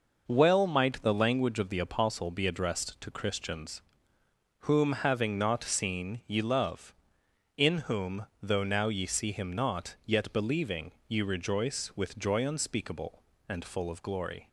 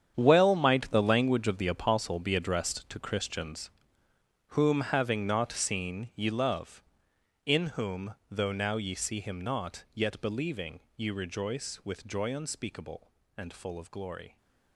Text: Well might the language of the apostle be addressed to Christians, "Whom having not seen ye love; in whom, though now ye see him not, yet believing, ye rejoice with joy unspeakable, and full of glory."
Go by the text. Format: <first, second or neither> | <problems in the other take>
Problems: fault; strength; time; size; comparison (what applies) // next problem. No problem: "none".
first | gets quieter; strong; throughout; 14 dB